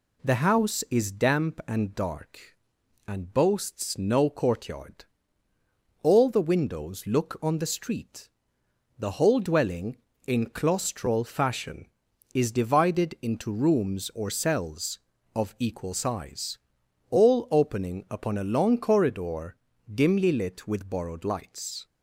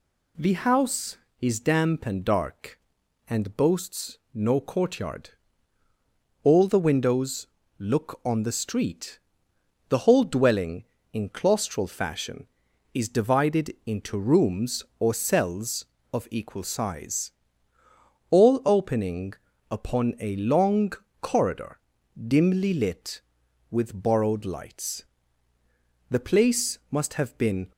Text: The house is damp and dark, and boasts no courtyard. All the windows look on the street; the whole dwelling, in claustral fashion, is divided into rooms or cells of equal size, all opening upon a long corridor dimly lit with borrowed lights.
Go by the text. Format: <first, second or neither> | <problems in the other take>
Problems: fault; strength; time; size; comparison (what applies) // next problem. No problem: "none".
first | pauses between "boasts" and "no"; slight; at 4.1 s; 0.16 s long // pauses between "windows" and "look"; slight; at 7.4 s; 0.32 s long // pauses between "opening" and "upon"; slight; at 19.3 s; 0.36 s long // pauses between "long" and "corridor"; slight; at 20.9 s; 0.30 s long // pauses between "corridor" and "dimly"; at 21.7 s; 0.36 s long; slight in the first // goes on to say "The place must have been"; from 26.1 s on; 1.6 s long